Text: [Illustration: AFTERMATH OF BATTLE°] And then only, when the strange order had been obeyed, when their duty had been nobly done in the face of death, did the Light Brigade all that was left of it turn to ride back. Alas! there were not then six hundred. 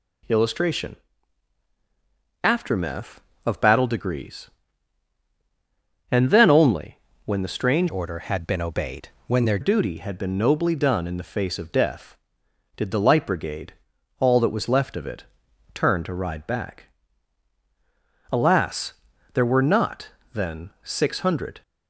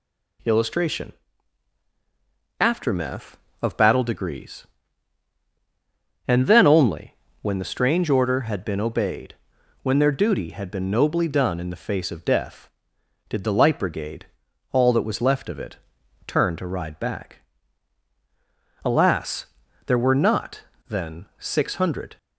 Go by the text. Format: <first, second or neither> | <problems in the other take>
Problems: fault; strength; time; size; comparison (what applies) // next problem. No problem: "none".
second | changes voice from "order" to "their"; from 7.8 to 9.5 s; 1.7 s long // pauses between "Brigade" and "all"; noticeable; at 13.7 s; 0.48 s long; noticeable in the second // pauses between "it" and "turn"; noticeable; at 15.2 s; 0.50 s long; noticeable in the second // pauses between "not" and "then"; slight; at 20.0 s; 0.24 s long; slight in the second